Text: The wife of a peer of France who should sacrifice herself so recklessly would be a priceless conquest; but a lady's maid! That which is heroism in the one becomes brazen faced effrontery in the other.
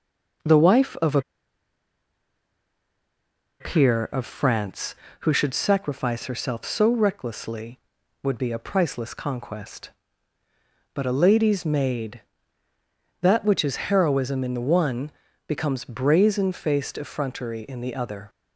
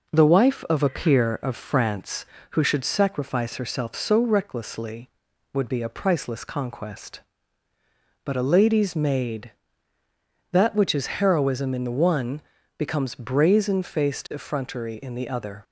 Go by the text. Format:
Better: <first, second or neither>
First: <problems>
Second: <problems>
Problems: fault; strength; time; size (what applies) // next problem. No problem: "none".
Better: second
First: pauses between "a" and "peer"; strong; at 1.1 s; 2.4 s long // pauses between "one" and "becomes"; at 15.0 s; 0.38 s long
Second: pauses between "one" and "becomes"; at 12.3 s; 0.38 s long